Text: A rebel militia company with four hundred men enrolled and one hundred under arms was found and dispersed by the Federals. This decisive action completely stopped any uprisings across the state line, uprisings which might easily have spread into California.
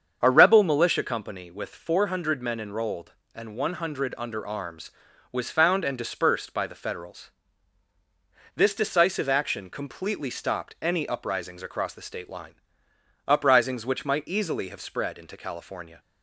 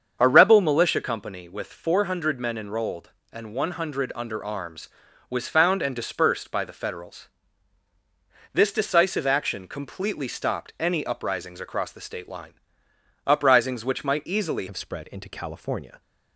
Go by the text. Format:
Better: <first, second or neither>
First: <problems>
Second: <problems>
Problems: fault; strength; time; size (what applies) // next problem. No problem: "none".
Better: first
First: starts louder than the rest; strong; until 1.2 s; 7 dB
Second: starts louder than the rest; strong; until 1.2 s; 7 dB // changes voice at "have"; from 14.6 s on; 1.4 s long